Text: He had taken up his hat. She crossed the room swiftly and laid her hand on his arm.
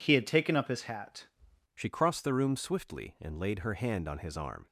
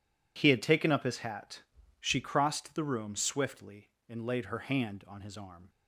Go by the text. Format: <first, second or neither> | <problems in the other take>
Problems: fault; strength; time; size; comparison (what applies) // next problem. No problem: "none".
second | changes voice at "She"; from 1.7 s on; 2.9 s long